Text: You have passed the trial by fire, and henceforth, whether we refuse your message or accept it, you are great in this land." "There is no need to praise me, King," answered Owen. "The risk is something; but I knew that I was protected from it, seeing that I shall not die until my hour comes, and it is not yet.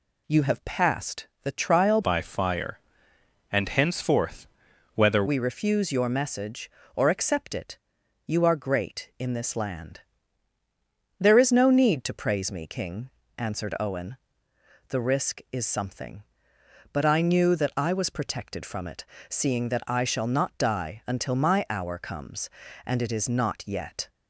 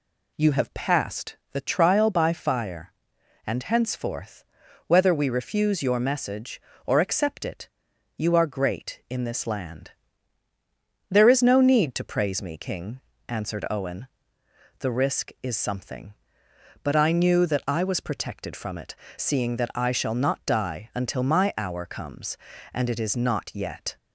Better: second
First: changes voice from "by" to "whether"; from 2.0 to 5.2 s; 3.2 s long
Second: none

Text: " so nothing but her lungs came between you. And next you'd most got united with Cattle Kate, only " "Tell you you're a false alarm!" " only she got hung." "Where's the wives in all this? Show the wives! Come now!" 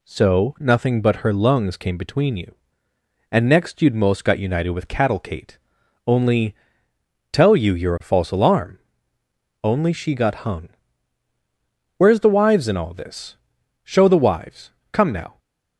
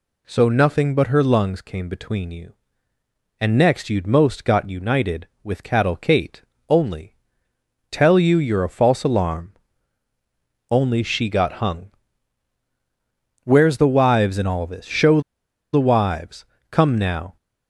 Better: first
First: none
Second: pauses between "Show" and "the"; noticeable; at 15.1 s; 0.53 s long

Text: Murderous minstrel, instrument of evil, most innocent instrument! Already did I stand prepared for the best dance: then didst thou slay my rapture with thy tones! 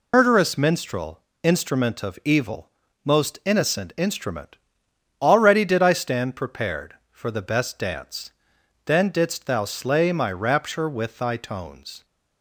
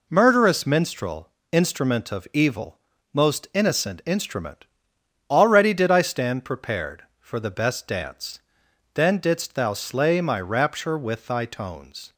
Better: second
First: loses the start of "Murderous"; at 0.1 s; 130 ms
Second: none

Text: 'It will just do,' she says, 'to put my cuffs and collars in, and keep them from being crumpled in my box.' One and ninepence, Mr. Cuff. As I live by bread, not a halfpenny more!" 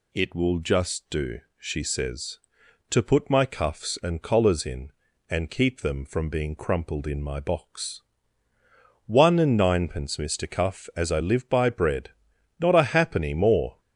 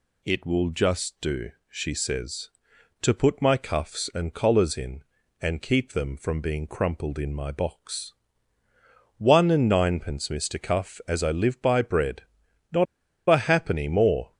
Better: first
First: none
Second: pauses between "not" and "a"; at 12.8 s; 0.44 s long

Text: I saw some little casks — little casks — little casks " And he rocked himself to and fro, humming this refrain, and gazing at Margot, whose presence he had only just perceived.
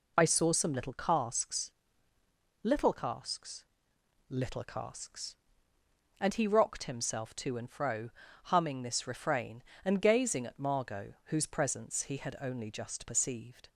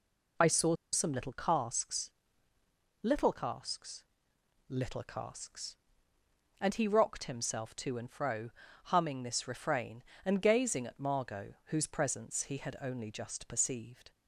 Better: first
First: none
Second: pauses between "saw" and "some"; slight; at 0.7 s; 0.18 s long

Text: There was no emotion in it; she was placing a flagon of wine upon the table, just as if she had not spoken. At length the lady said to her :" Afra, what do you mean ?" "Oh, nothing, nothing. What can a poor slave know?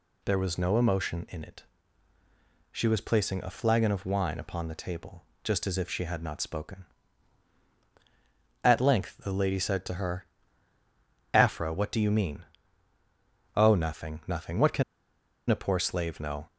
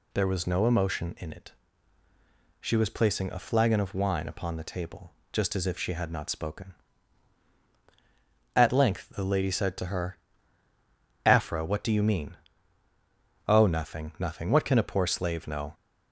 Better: second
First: pauses between "can" and "a"; noticeable; at 14.8 s; 0.67 s long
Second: none

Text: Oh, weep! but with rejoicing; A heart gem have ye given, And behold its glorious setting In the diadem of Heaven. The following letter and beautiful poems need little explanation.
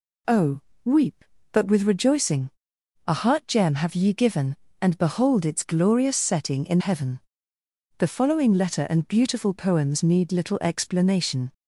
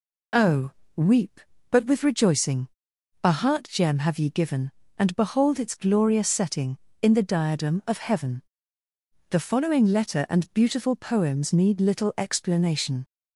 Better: second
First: skips "the diadem of"; at 6.7 s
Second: none

